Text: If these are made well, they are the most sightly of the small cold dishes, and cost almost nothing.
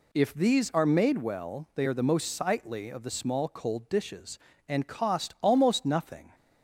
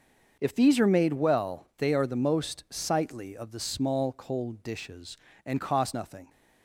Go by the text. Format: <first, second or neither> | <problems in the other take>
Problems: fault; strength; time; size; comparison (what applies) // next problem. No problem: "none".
first | starts louder than the rest; until 1.4 s; 6.5 dB // skips "almost"; at 5.9 s